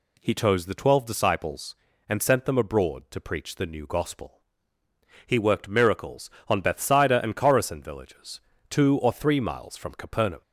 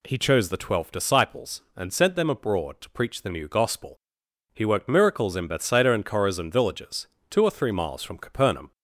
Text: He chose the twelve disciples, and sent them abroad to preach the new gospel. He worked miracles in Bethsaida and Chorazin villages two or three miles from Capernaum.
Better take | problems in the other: second | says "on" for "in"; at 6.4 s // pauses between "villages" and "two"; slight; at 8.3 s; 0.30 s long; slight in the second

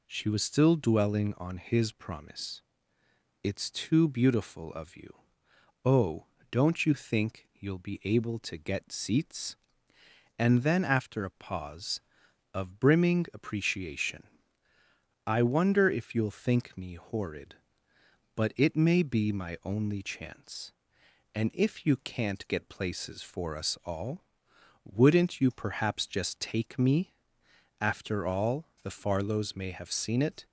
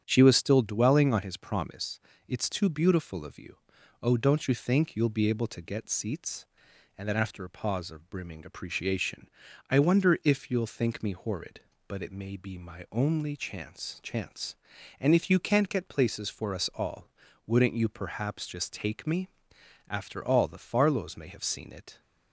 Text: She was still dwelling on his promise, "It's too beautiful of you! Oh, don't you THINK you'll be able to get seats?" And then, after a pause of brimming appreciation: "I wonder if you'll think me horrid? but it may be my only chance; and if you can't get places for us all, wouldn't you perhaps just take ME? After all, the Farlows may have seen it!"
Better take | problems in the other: first | starts louder than the rest; strong; until 1.0 s; 9 dB // says "chance" twice; at 14.0 s

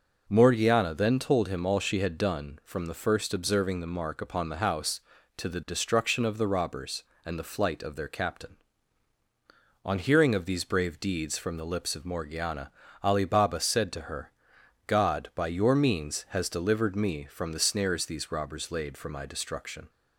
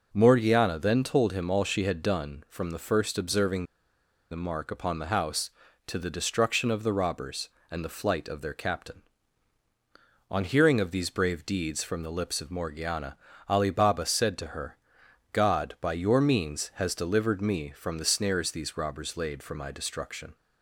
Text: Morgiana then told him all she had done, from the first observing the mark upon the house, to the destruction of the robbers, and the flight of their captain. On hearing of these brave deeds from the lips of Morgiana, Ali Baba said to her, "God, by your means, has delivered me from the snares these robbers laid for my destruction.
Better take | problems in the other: first | pauses between "observing" and "the"; noticeable; at 3.6 s; 0.67 s long

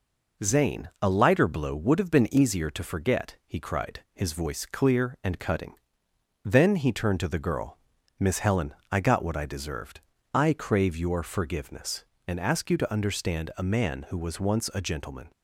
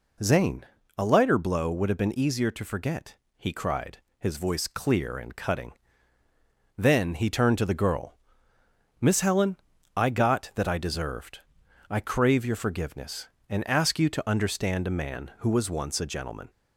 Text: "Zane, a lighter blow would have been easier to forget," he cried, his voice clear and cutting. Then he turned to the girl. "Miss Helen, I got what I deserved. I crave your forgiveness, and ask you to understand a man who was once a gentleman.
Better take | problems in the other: first | says "that" for "what"; at 10.5 s

